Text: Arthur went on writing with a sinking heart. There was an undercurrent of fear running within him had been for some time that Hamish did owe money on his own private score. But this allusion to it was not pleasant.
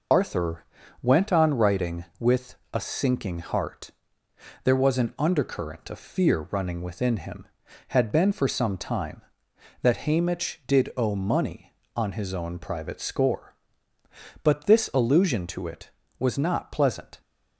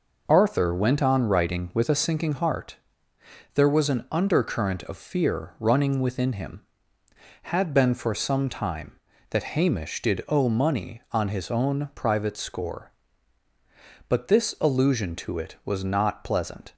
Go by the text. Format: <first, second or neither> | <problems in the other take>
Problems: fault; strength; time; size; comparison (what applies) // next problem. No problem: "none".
second | loses the start of "Arthur"; at 0.1 s; 75 ms // pauses between "Arthur" and "went"; slight; at 0.6 s; 0.36 s long // pauses between "with" and "a"; slight; at 2.5 s; 0.16 s long